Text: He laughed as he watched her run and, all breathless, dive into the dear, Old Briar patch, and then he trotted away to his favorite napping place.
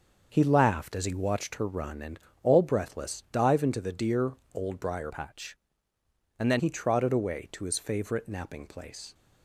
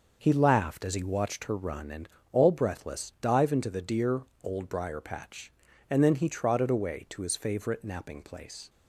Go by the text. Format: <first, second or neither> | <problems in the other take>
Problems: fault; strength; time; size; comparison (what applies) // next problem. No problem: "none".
second | starts louder than the rest; until 1.3 s; 6.5 dB // changes voice from "patch" to "then"; from 5.1 to 6.5 s; 1.4 s long